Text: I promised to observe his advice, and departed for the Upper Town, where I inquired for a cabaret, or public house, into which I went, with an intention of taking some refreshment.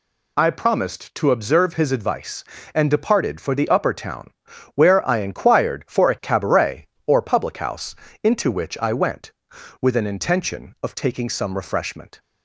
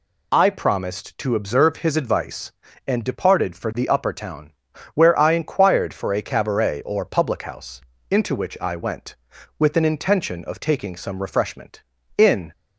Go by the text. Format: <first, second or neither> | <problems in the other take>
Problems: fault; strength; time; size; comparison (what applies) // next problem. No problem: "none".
first | goes on to say "In"; slight; from 12.1 s on; 0.34 s long